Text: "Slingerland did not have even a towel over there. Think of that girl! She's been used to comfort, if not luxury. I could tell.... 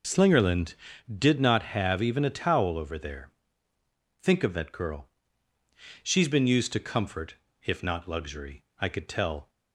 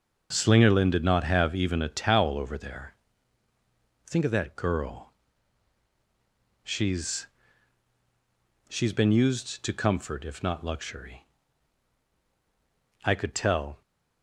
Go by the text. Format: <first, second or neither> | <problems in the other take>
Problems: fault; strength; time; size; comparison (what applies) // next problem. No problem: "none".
first | starts louder than the rest; noticeable; until 1.3 s; 6 dB // says "She's" twice; at 8.6 s